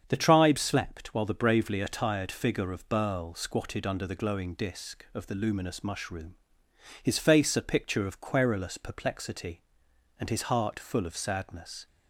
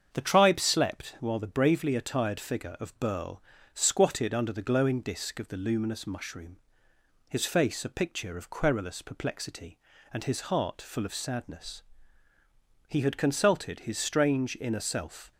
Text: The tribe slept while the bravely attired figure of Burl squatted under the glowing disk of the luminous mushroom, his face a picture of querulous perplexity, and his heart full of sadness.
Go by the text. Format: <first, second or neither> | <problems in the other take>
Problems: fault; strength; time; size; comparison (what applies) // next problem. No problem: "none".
first | starts louder than the rest; strong; until 1.1 s; 7.5 dB; strong in the first // pauses between "Burl" and "squatted"; slight; at 3.4 s; 0.32 s long // goes on to say "He had consulted his strange inner self"; strong; from 12.8 s on; 2.4 s long